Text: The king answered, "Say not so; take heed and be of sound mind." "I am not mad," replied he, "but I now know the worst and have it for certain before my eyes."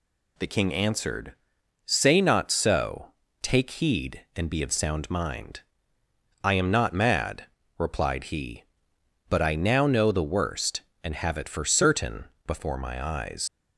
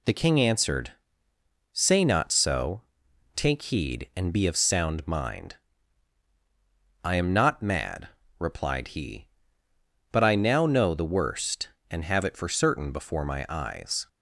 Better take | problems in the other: second | pauses between "certain" and "before"; slight; at 12.2 s; 0.20 s long // leaves "eyes" unfinished; at 13.4 s; 85 ms

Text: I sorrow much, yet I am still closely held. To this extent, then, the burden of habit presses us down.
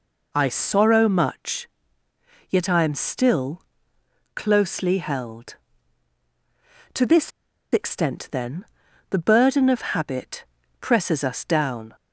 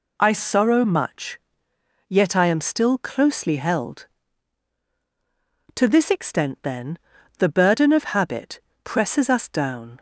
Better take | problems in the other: second | pauses between "still" and "closely"; noticeable; at 3.6 s; 0.74 s long // pauses between "this" and "extent"; at 7.3 s; 0.43 s long // pauses between "habit" and "presses"; slight; at 10.4 s; 0.34 s long; slight in the second

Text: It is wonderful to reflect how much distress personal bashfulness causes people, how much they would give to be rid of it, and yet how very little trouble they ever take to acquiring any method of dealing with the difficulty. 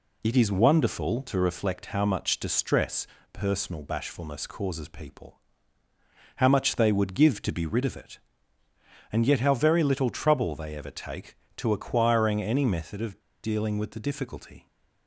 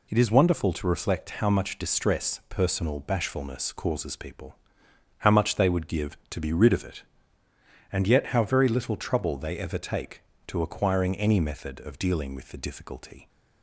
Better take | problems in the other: second | pauses between "distress" and "personal"; slight; at 3.0 s; 0.26 s long // pauses between "of" and "dealing"; slight; at 13.2 s; 0.23 s long

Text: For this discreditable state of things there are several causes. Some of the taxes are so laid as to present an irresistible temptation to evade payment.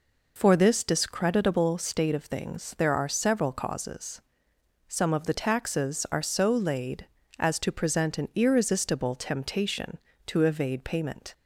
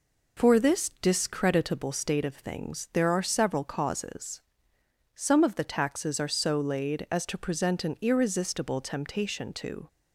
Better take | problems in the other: first | stops before "evade payment"; at 9.8 s

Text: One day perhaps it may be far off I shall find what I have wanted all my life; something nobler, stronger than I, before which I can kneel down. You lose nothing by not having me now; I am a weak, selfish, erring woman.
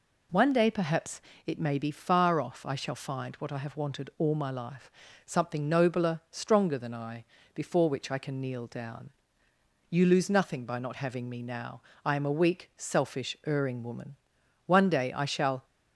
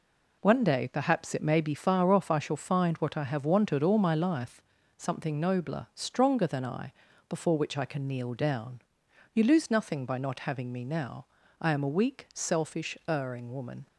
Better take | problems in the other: second | pauses between "perhaps" and "it"; slight; at 1.2 s; 0.24 s long // goes on to say "One day I shall"; noticeable; from 14.6 s on; 0.98 s long

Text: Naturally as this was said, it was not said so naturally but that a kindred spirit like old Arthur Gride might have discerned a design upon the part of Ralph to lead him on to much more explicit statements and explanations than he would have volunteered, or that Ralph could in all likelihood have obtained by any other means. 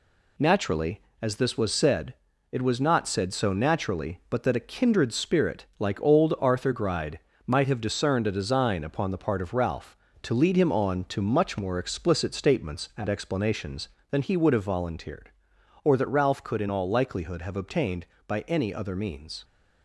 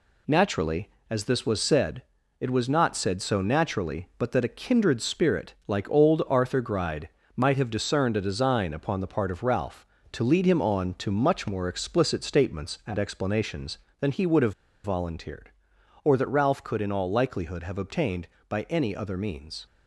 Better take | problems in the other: first | pauses between "Gride" and "might"; slight; at 7.0 s; 0.28 s long; slight in the first // pauses between "have" and "volunteered"; slight; at 14.5 s; 0.31 s long

